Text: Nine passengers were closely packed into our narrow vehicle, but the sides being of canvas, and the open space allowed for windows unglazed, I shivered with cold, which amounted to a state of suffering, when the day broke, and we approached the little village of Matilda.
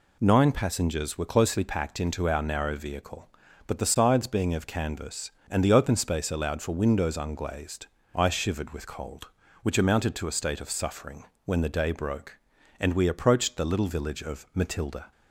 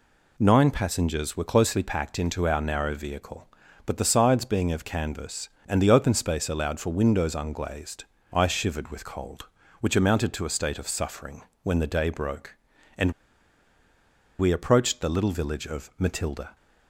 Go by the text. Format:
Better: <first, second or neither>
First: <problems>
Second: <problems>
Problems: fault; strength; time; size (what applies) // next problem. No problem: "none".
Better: first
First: none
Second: pauses between "and" and "we"; strong; at 13.1 s; 1.2 s long